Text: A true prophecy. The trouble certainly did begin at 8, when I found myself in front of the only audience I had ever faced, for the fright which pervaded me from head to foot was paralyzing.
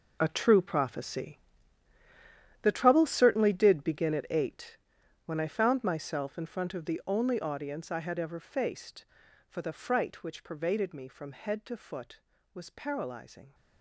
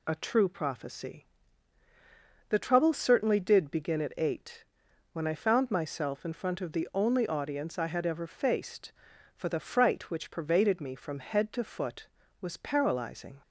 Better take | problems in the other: second | gets quieter; strong; throughout; 13.5 dB

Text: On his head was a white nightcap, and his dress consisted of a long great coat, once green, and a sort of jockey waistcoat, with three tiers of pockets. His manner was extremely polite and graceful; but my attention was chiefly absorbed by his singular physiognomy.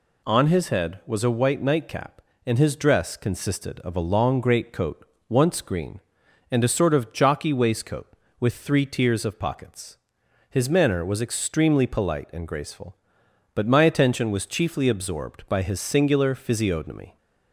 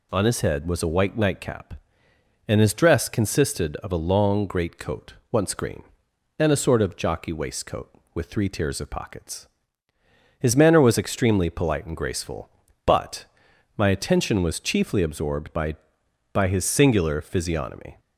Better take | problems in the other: first | pauses between "but" and "my"; noticeable; at 13.2 s; 0.52 s long // says "by" twice; at 16.3 s

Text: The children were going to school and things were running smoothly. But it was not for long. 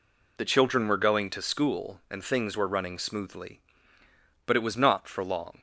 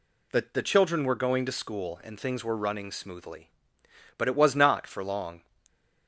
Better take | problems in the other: first | says "The" twice; at 0.5 s

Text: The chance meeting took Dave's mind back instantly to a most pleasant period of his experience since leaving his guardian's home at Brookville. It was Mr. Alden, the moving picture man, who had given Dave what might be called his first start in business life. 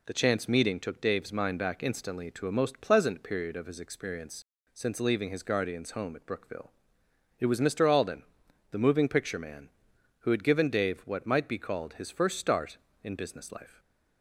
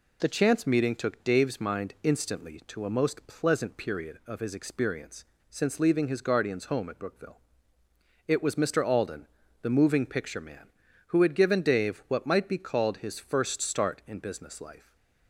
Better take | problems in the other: first | skips "back"; at 1.9 s // pauses between "experience" and "since"; slight; at 5.2 s; 0.24 s long; slight in the first // stays silent after the last word; slight; from 14.7 s on; 0.5 s long

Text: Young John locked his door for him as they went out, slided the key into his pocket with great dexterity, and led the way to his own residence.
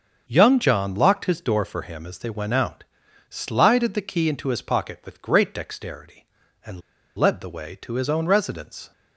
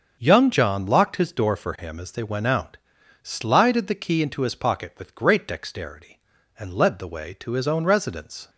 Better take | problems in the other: second | starts louder than the rest; until 1.2 s; 6.5 dB; also in the second // pauses between "and" and "led"; slight; at 6.8 s; 0.35 s long

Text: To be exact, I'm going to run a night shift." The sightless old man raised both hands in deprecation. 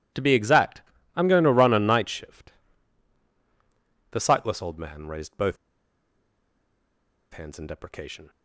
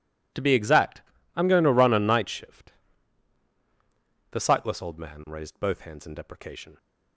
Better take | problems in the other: second | pauses between "both" and "hands"; strong; at 5.5 s; 1.7 s long

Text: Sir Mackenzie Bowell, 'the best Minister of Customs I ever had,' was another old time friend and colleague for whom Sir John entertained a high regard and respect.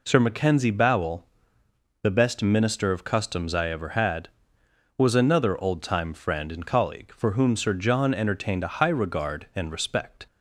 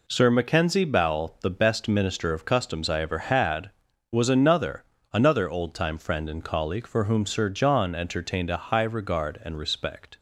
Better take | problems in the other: first | says "another" twice; at 5.1 s

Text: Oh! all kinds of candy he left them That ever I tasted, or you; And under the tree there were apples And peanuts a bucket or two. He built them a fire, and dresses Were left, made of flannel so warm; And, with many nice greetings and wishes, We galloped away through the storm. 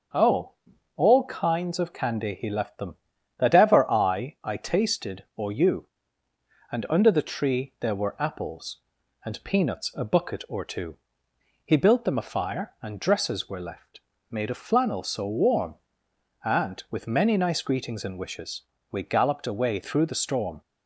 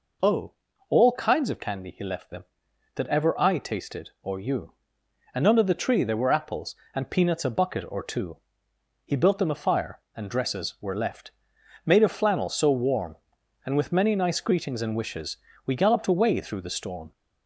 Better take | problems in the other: second | starts louder than the rest; until 1.6 s; 7 dB // says "I" twice; at 4.4 s

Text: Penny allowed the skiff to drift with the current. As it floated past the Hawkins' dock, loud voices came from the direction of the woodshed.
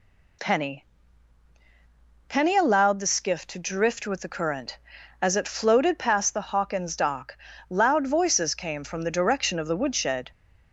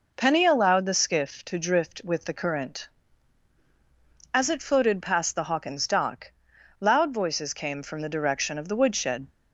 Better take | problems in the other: second | says "Penny" twice; at 2.2 s

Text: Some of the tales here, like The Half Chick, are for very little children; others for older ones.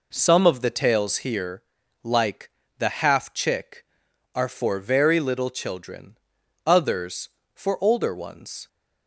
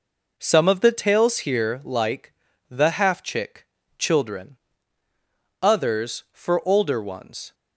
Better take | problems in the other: first | pauses between "like" and "The"; at 2.3 s; 0.38 s long; slight in the first // skips "are for very little"; at 3.8 s

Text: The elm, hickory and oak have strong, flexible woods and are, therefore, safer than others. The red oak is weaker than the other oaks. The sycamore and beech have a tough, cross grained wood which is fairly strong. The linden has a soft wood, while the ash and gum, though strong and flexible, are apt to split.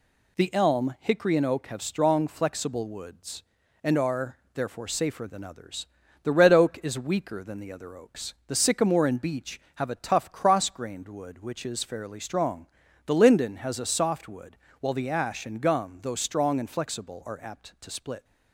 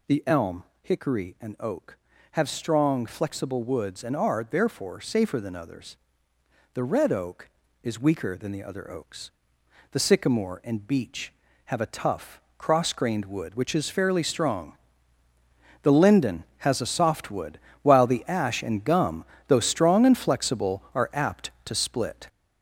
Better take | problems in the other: first | gets louder; throughout; 6 dB

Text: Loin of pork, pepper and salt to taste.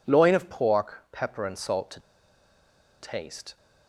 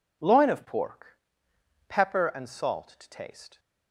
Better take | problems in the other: second | pauses between "to" and "taste"; at 1.9 s; 1.0 s long

